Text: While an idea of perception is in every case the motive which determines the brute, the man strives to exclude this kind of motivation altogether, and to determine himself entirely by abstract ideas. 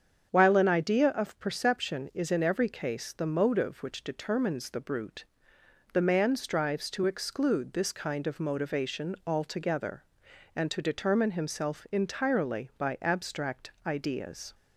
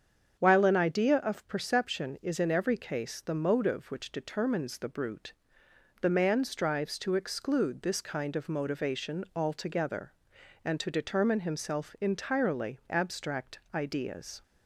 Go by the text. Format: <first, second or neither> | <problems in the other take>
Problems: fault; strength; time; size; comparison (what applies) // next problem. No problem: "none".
first | starts louder than the rest; strong; until 1.4 s; 7.5 dB; strong in the first // skips "by"; at 12.8 s // pauses between "abstract" and "ideas"; slight; at 13.5 s; 0.16 s long; slight in the first